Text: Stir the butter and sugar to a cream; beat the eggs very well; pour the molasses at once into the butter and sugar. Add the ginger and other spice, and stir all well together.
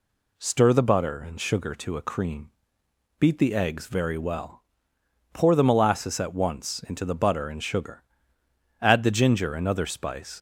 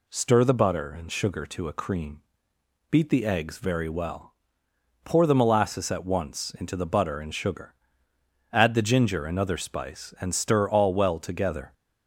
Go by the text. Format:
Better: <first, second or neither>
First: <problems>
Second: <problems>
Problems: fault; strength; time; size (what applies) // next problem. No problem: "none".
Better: second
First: stops before "and stir all well together"; at 10.3 s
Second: none